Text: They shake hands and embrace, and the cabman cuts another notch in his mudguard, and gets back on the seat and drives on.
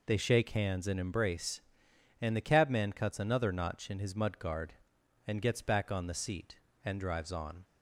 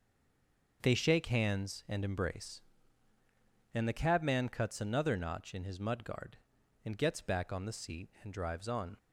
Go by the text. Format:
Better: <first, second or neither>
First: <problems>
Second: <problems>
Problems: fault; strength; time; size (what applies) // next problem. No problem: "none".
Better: first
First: none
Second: stays silent before the first word; slight; until 0.8 s; 0.8 s long